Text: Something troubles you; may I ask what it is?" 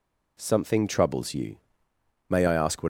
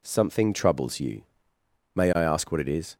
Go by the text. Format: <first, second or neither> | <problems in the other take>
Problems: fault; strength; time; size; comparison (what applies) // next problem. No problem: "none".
second | stops before "it is"; at 2.8 s